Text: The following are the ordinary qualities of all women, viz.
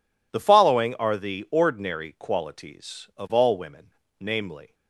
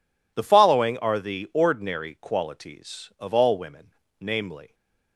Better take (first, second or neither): neither